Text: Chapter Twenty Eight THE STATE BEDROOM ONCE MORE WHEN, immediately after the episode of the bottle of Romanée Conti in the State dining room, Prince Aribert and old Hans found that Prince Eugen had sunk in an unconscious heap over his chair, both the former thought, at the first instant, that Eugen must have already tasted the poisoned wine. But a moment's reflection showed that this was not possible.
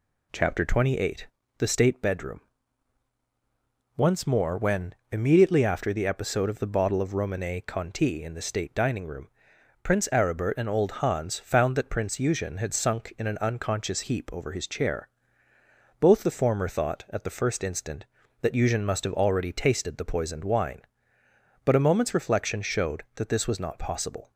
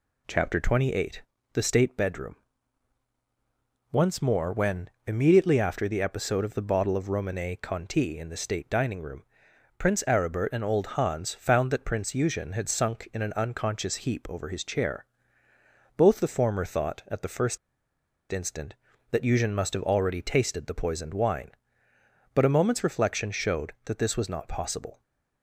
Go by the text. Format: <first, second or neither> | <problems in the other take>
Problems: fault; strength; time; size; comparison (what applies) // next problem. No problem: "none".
first | pauses between "Eight" and "THE"; slight; at 1.2 s; 0.32 s long; slight in the first // pauses between "BEDROOM" and "ONCE"; strong; at 2.3 s; 1.5 s long; strong in the first // pauses between "first" and "instant"; noticeable; at 17.5 s; 0.73 s long